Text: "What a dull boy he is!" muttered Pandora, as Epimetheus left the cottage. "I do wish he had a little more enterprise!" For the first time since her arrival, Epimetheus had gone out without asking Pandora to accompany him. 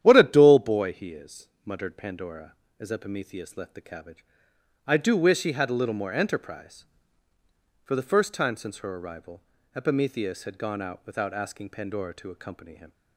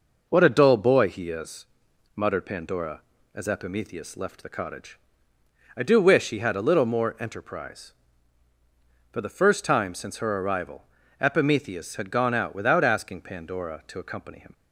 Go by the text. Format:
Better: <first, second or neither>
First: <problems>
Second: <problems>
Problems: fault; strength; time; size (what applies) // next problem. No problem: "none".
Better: second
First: starts louder than the rest; strong; until 1.0 s; 10.5 dB // says "cabbage" for "cottage"; at 3.8 s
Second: none